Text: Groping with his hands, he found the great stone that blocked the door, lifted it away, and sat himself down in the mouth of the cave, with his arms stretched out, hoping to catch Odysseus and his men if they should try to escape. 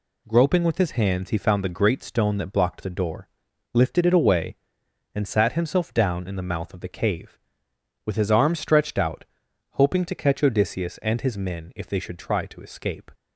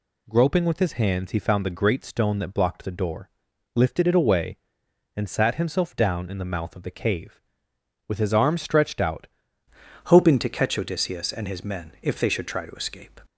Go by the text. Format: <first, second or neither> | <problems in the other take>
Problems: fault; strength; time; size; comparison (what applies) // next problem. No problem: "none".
first | changes voice at "hoping"; from 10.0 s on; 3.1 s long